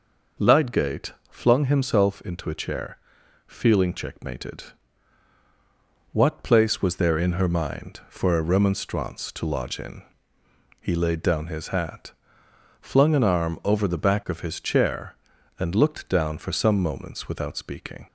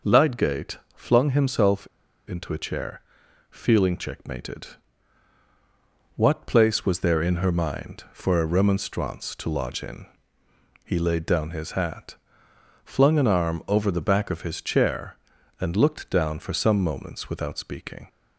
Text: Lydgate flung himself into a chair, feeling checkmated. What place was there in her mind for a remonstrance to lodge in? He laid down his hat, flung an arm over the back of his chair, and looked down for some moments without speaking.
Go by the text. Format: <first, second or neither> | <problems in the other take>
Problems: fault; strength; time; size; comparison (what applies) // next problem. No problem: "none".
first | pauses between "Lydgate" and "flung"; slight; at 0.7 s; 0.18 s long; slight in the first // pauses between "himself" and "into"; at 1.8 s; 0.41 s long